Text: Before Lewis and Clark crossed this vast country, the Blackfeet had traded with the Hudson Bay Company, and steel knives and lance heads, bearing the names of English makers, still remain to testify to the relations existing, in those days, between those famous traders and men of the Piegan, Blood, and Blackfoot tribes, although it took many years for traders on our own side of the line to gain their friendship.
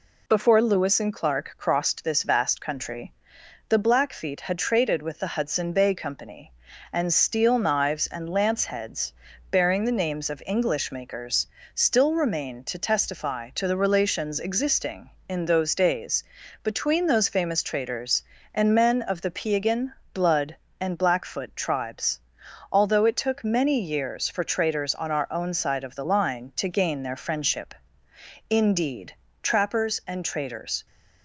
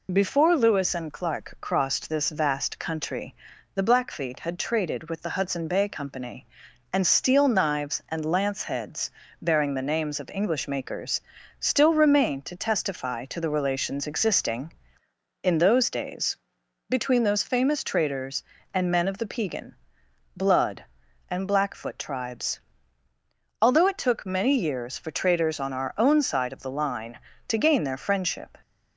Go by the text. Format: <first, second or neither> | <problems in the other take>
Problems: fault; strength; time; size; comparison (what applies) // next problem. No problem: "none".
second | goes on to say "Indeed trappers and traders"; strong; from 28.4 s on; 2.3 s long